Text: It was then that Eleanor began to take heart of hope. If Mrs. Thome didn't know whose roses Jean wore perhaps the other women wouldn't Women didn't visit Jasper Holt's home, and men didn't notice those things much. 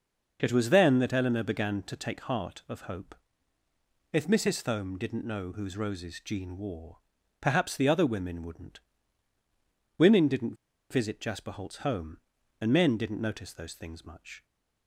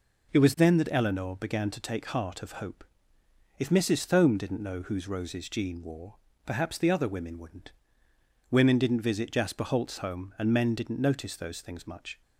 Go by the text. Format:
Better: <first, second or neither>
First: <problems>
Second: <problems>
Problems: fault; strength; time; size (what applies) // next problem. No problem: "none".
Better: second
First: pauses between "wore" and "perhaps"; at 6.9 s; 0.42 s long // pauses between "wouldn't" and "Women"; at 8.8 s; 1.1 s long // pauses between "didn't" and "visit"; at 10.5 s; 0.36 s long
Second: pauses between "wore" and "perhaps"; slight; at 6.1 s; 0.28 s long // pauses between "wouldn't" and "Women"; noticeable; at 7.7 s; 0.78 s long